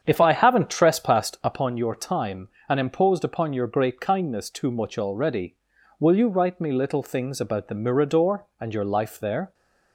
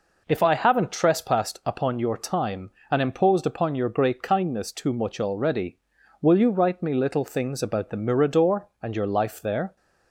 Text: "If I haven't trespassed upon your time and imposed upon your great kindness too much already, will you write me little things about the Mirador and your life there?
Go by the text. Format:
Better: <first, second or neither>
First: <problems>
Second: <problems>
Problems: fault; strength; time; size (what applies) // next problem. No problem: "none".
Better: second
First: starts louder than the rest; strong; until 1.6 s; 8 dB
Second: none